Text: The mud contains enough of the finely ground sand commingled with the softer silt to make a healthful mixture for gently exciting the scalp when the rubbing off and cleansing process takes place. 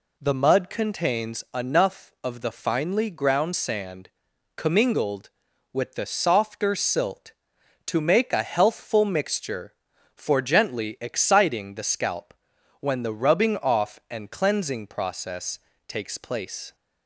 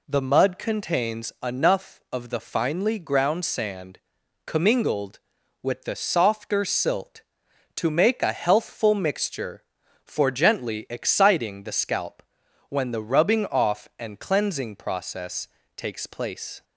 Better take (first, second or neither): neither